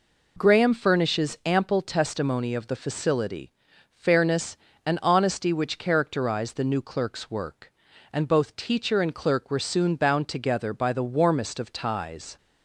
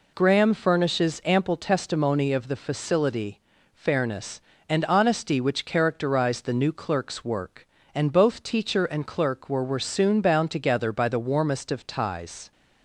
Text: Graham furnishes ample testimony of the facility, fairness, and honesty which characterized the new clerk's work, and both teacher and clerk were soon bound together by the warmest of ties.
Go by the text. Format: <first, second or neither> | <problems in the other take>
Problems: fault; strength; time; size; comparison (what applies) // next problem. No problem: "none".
first | says "were" twice; at 9.6 s